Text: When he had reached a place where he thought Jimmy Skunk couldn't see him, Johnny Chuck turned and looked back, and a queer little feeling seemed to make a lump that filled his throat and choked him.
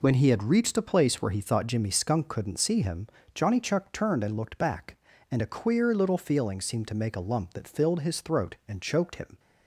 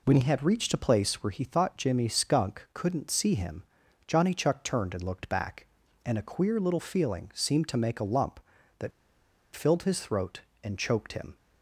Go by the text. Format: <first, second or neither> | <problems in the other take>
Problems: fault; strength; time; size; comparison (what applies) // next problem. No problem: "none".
first | pauses between "that" and "filled"; noticeable; at 8.9 s; 0.63 s long